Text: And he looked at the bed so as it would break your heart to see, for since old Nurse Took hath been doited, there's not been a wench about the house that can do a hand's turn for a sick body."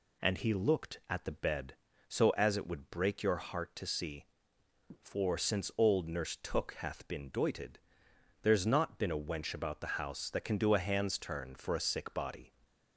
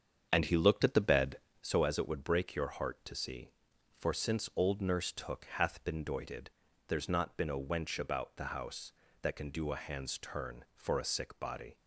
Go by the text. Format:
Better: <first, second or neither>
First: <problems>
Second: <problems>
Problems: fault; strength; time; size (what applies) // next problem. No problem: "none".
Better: first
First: none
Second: starts louder than the rest; strong; until 1.7 s; 7.5 dB